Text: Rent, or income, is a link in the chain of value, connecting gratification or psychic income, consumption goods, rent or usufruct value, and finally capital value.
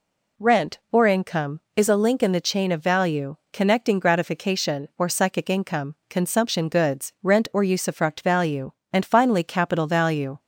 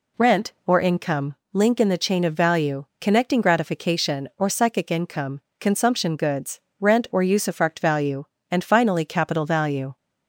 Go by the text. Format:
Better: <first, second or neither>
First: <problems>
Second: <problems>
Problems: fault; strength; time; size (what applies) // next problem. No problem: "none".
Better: first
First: none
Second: skips "is a"; at 1.4 s